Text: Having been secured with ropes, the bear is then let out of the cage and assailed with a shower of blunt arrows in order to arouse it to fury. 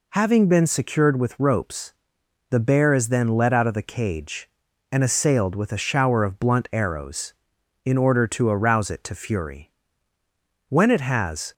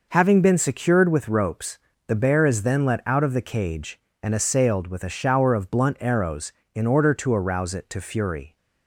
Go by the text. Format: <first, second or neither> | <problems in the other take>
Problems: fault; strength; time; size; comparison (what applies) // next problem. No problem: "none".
second | goes on to say "When it has"; noticeable; from 10.6 s on; 0.84 s long